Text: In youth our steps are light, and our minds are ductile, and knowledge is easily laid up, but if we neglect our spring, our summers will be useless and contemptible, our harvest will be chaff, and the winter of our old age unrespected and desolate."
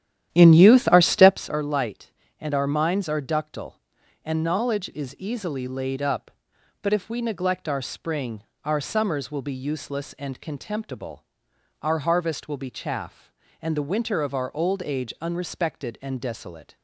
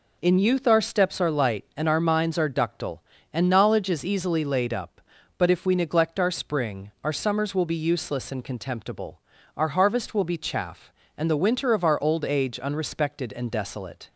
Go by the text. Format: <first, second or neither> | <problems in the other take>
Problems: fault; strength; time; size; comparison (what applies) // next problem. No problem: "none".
second | starts louder than the rest; strong; until 1.4 s; 11.5 dB